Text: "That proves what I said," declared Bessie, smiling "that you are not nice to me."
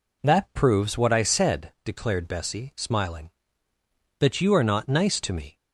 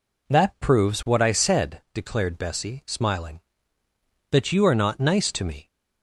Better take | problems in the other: neither | none

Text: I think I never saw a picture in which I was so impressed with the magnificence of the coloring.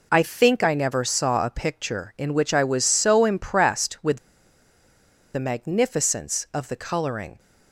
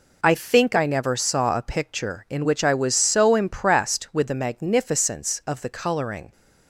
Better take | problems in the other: second | pauses between "with" and "the"; at 4.1 s; 1.1 s long

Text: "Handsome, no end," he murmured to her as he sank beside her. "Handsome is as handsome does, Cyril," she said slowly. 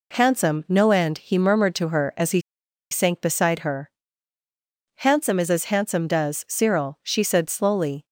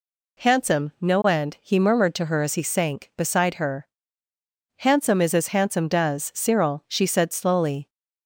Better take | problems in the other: second | pauses between "he" and "sank"; noticeable; at 2.4 s; 0.49 s long

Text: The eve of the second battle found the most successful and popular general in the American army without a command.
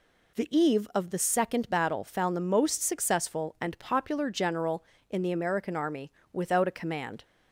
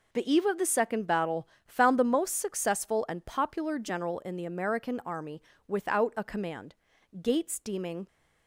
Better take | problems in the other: first | pauses between "battle" and "found"; slight; at 1.4 s; 0.20 s long // pauses between "army" and "without"; slight; at 5.4 s; 0.28 s long; slight in the first // goes on to say "Gates deeming"; noticeable; from 7.2 s on; 0.86 s long

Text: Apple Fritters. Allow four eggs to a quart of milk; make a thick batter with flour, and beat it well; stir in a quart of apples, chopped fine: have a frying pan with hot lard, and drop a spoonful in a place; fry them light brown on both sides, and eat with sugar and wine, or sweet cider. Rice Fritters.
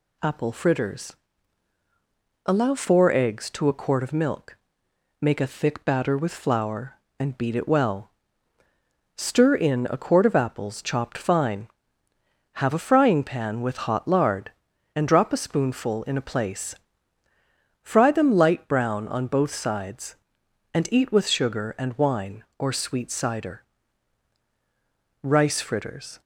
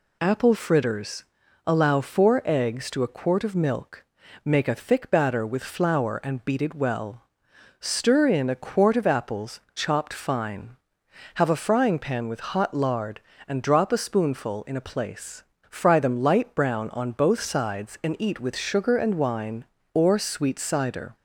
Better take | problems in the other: first | stops before "Rice Fritters"; at 21.1 s

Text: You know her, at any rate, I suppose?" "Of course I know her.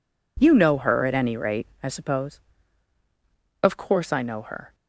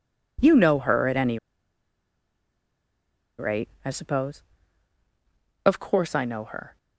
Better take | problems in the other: first | pauses between "any" and "rate"; strong; at 1.3 s; 2.0 s long

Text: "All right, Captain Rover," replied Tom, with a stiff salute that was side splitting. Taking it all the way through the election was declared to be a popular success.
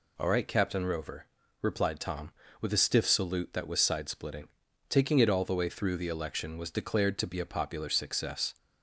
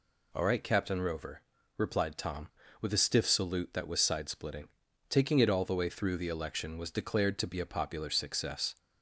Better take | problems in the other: neither | none

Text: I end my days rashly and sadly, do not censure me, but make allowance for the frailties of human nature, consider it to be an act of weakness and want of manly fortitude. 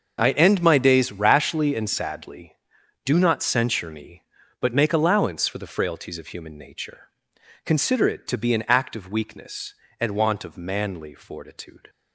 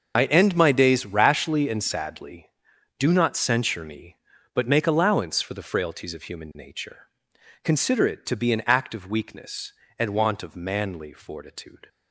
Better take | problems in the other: first | loses the start of "I"; at 0.1 s; 30 ms // starts louder than the rest; until 1.1 s; 6 dB; also in the first

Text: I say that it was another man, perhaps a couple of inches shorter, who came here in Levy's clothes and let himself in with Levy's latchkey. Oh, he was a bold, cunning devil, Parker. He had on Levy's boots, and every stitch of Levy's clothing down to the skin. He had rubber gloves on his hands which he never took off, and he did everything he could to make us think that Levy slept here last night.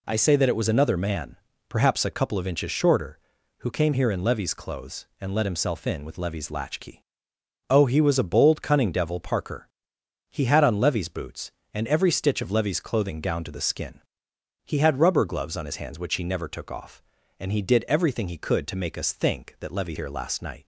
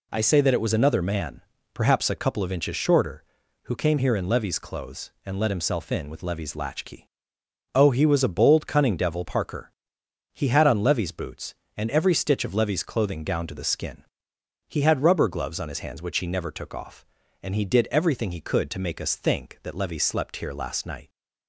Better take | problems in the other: second | skips "slept"; at 19.9 s

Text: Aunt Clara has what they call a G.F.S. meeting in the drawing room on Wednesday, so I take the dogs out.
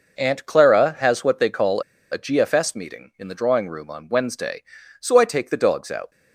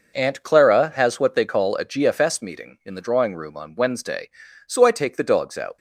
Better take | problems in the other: second | pauses between "call" and "a"; slight; at 1.8 s; 0.29 s long

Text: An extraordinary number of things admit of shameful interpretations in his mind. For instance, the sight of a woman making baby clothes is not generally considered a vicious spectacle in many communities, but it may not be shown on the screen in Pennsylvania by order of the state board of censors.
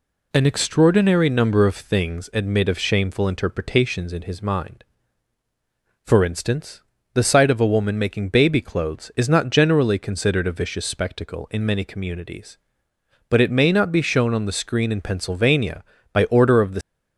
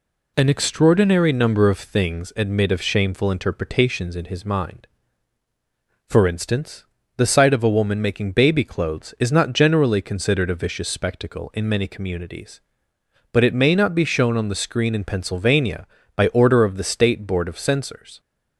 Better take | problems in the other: second | stops before "state board of censors"; at 16.8 s

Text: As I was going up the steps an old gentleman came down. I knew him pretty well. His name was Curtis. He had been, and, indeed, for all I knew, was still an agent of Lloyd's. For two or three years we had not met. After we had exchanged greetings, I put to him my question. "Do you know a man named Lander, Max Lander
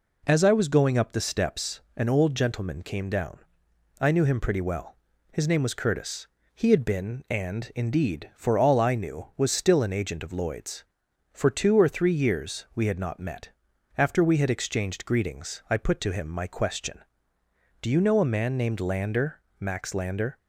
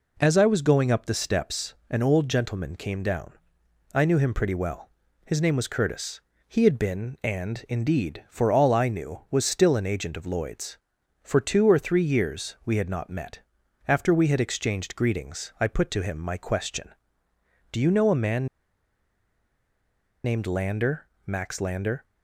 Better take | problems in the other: first | pauses between "steps" and "an"; slight; at 1.7 s; 0.16 s long; slight in the first // pauses between "man" and "named"; strong; at 18.4 s; 1.7 s long

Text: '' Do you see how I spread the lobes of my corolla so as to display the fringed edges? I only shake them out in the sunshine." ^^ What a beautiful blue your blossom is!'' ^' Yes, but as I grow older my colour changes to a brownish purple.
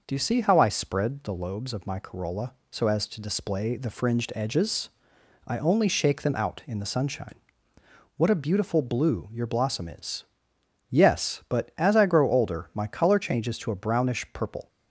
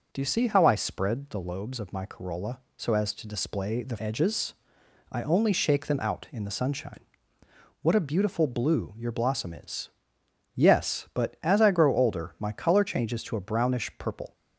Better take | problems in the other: first | skips "fringed"; at 3.9 s

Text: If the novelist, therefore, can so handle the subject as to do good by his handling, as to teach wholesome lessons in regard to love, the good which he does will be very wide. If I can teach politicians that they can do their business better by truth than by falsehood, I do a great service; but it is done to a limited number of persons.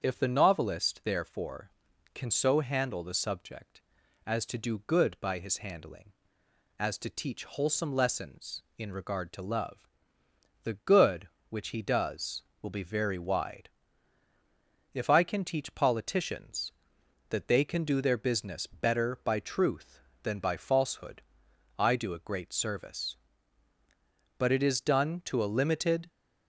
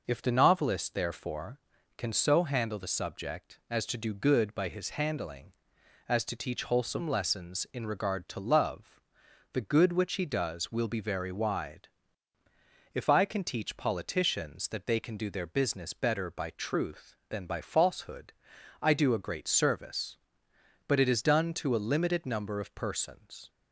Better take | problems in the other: second | starts louder than the rest; strong; until 1.0 s; 7 dB // stops before "number of persons"; at 26.0 s

